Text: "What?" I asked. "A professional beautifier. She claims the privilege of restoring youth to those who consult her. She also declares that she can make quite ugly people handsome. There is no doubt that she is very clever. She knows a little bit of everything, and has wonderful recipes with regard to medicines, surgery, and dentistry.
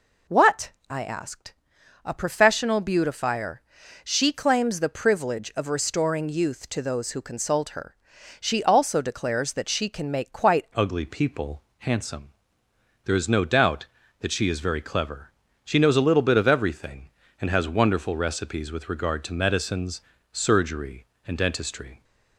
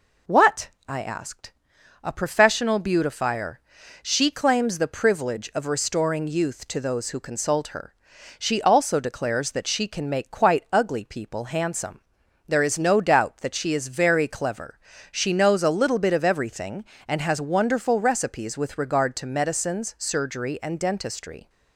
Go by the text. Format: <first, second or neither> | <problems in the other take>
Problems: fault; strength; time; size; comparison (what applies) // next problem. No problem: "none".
second | changes voice at "ugly"; from 10.7 s on; 11.3 s long // pauses between "people" and "handsome"; slight; at 11.6 s; 0.18 s long